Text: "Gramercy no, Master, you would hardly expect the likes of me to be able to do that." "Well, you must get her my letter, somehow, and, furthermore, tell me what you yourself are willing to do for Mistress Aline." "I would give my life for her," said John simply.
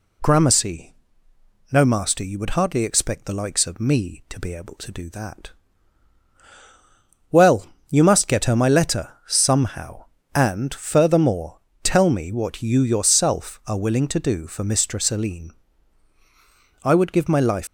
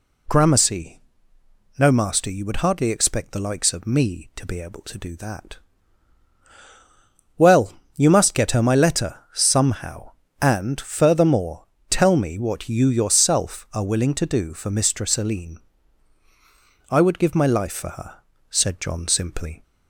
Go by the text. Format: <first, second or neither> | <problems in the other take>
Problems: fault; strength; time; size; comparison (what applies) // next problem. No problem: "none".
second | pauses between "Gramercy" and "no"; noticeable; at 0.9 s; 0.78 s long; noticeable in the second // stops before "for her said John simply"; at 17.6 s